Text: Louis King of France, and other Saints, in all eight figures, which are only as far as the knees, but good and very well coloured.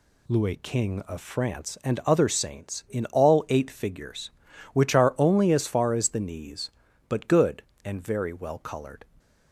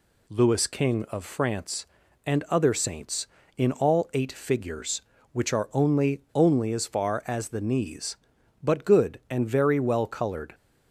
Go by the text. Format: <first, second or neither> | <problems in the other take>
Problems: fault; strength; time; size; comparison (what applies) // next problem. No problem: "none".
first | says "only" twice; at 6.3 s